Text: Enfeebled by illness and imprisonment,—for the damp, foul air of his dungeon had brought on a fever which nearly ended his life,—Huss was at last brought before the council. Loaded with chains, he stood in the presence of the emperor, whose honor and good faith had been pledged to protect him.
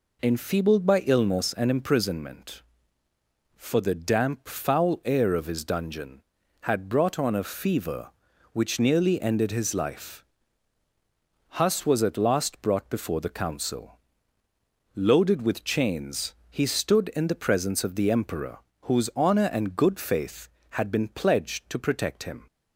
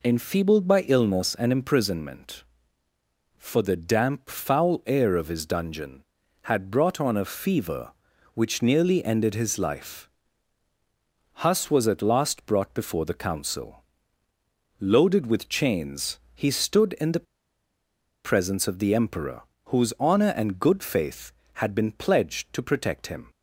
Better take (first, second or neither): first